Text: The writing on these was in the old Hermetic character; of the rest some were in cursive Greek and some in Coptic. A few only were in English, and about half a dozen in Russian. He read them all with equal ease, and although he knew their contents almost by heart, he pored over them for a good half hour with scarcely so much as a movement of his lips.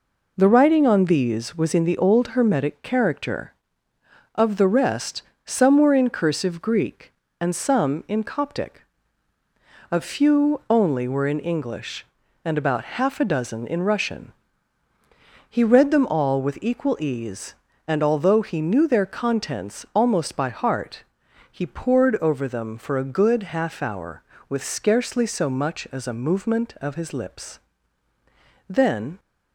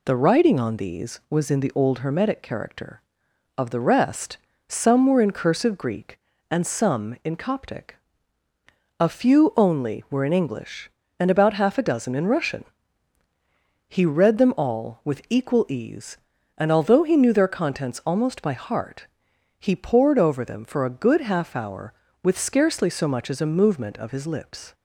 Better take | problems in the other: second | pauses between "rest" and "some"; slight; at 5.2 s; 0.24 s long; slight in the second // goes on to say "Then"; from 28.6 s on; 0.52 s long

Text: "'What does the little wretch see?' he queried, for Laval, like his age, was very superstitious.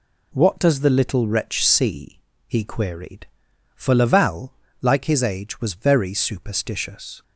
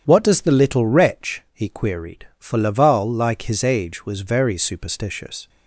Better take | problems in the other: first | starts louder than the rest; strong; until 1.0 s; 9 dB // skips "see"; at 1.4 s

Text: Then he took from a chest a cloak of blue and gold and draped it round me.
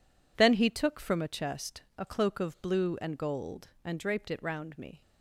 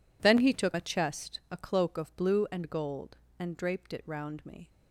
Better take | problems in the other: first | skips "from"; at 0.7 s

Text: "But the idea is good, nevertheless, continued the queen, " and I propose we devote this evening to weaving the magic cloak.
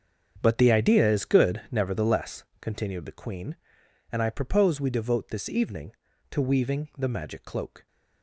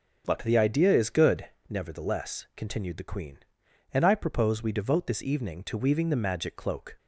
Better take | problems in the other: second | gets quieter; strong; throughout; 14 dB

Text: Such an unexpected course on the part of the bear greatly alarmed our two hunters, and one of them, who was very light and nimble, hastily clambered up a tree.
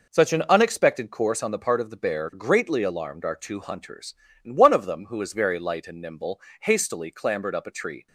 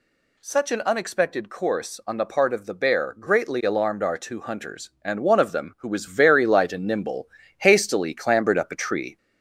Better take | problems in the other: first | gets louder; slight; throughout; 3 dB

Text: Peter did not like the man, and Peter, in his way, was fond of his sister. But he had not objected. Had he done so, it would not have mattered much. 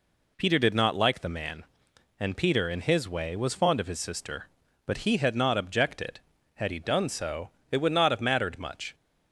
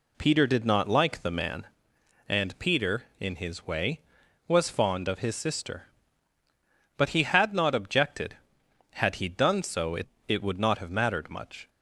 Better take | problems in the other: first | says "it" twice; at 10.2 s

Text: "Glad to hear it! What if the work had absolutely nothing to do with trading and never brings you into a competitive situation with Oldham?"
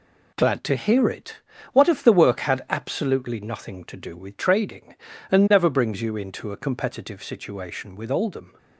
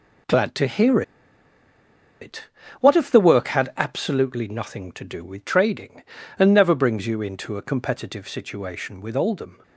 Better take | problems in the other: first | pauses between "hear" and "it"; at 1.0 s; 1.1 s long

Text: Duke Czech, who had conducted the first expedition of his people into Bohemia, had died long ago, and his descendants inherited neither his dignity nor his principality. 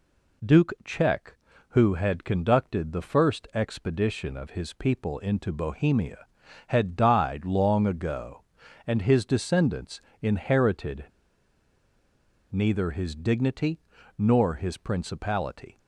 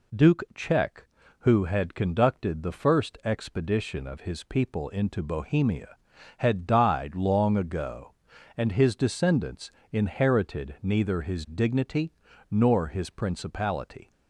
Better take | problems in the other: second | pauses between "descendants" and "inherited"; slight; at 9.9 s; 0.22 s long; slight in the second // pauses between "inherited" and "neither"; strong; at 11.0 s; 1.4 s long // pauses between "dignity" and "nor"; at 13.7 s; 0.38 s long; also in the second

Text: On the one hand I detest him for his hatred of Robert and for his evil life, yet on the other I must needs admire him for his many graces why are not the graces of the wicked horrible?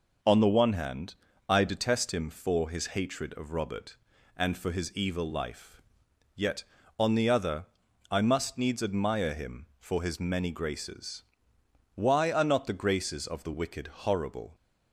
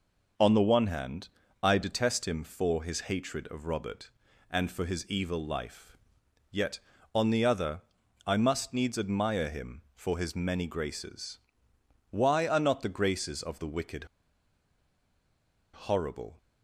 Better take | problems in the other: first | pauses between "hand" and "I"; slight; at 1.2 s; 0.34 s long; slight in the first // pauses between "other" and "I"; noticeable; at 7.7 s; 0.46 s long; noticeable in the first // pauses between "graces" and "why"; noticeable; at 11.3 s; 0.74 s long; noticeable in the first // pauses between "wicked" and "horrible"; strong; at 14.0 s; 1.6 s long

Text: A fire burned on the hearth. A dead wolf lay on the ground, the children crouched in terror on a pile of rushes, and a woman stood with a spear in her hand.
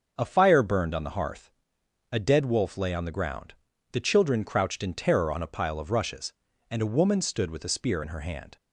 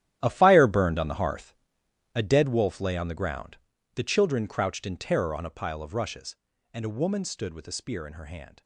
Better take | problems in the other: first | gets quieter; strong; throughout; 14.5 dB // starts louder than the rest; strong; until 1.2 s; 12 dB; also in the first

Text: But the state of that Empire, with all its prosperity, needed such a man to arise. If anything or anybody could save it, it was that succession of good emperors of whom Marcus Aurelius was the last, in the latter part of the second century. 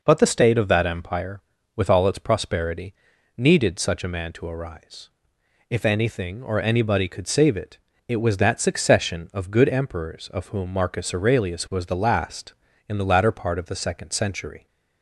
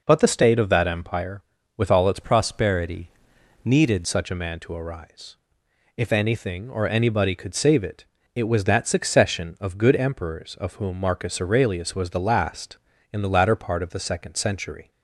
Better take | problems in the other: first | changes voice from "prosperity" to "needed"; from 2.2 to 4.0 s; 1.8 s long

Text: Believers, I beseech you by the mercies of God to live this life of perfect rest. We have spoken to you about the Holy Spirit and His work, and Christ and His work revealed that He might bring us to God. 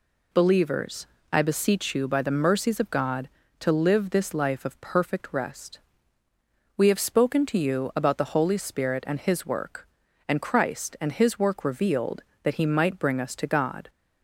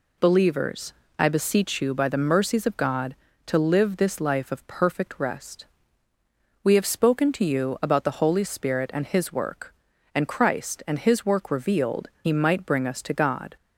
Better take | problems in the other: first | skips "that"; at 12.1 s

